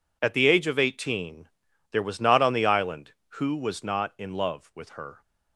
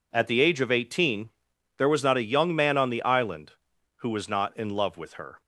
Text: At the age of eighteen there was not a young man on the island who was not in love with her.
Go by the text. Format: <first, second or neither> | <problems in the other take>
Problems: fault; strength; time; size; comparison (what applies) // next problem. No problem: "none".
second | pauses between "eighteen" and "there"; at 1.4 s; 0.42 s long; noticeable in the second // skips "a young man"; at 2.4 s